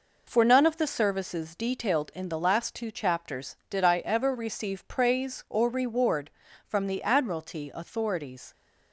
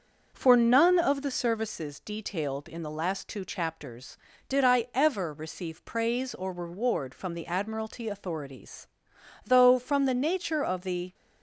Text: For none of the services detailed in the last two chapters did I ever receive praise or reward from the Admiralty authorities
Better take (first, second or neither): first